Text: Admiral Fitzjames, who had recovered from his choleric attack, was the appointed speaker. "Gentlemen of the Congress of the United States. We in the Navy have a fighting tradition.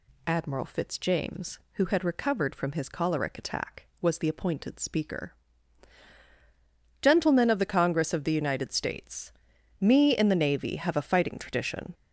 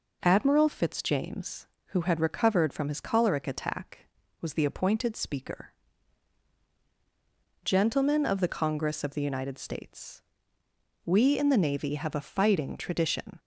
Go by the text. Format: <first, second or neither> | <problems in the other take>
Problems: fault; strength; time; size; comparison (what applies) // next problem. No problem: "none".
second | says "Me" for "We"; at 9.7 s